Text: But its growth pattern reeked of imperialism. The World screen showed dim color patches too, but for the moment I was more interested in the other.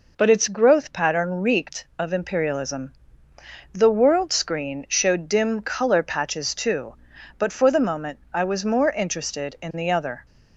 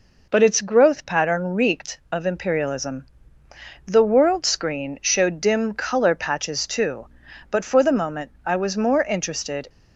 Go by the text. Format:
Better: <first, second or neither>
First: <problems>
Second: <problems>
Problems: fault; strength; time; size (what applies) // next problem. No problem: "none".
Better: first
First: none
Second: stops before "in the other"; at 9.6 s